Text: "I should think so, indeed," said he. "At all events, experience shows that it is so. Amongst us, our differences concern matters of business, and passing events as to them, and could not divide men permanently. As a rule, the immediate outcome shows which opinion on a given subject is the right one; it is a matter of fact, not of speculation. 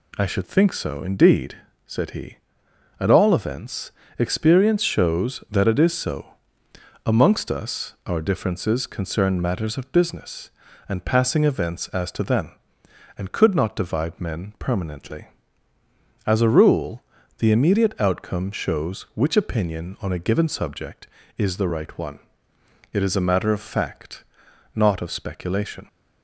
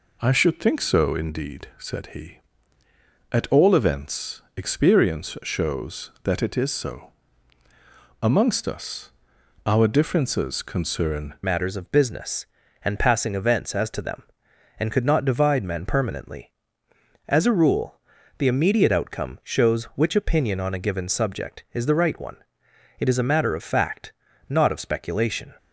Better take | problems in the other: first | changes voice at "matters"; from 11.4 s on; 14.1 s long

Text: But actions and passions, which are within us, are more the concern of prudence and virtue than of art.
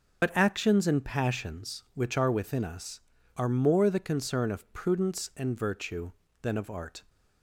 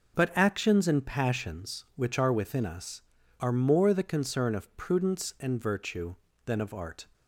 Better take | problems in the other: second | loses the start of "But"; at 0.2 s; 75 ms

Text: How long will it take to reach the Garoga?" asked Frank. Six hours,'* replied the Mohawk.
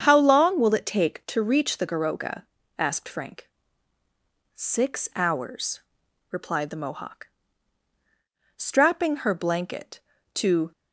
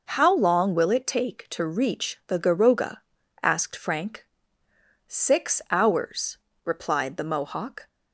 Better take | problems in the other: second | starts louder than the rest; strong; until 1.0 s; 7.5 dB // goes on to say "Strapping her blanket to"; strong; from 8.5 s on; 2.1 s long

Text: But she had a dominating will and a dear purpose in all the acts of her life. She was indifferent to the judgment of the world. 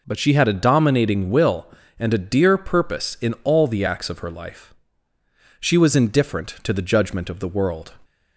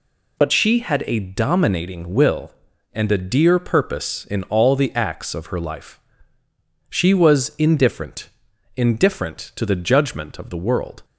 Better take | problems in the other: first | says "indifferent" twice; at 8.7 s

